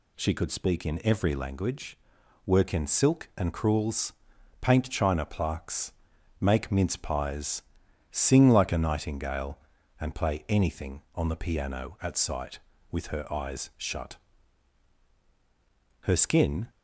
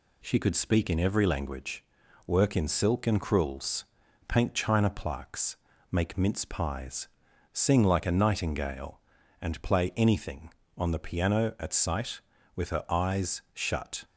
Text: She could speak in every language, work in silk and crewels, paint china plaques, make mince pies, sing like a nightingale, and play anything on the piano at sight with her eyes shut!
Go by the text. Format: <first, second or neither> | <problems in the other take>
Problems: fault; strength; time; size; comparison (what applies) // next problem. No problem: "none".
second | goes on to say "Her skin"; noticeable; from 16.0 s on; 0.66 s long